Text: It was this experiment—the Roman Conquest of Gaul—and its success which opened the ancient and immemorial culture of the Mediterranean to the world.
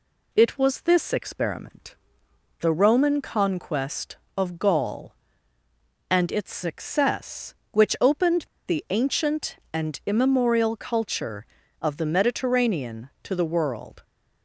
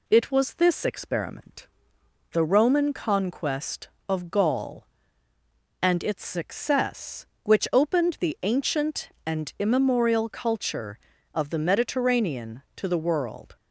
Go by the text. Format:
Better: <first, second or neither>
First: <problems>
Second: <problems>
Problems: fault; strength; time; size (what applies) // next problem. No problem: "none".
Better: second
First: pauses between "opened" and "the"; slight; at 8.4 s; 0.21 s long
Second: none